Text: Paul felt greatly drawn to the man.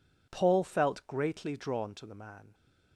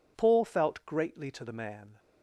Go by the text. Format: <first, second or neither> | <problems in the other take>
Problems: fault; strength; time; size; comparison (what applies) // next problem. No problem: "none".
first | skips "drawn"; at 1.3 s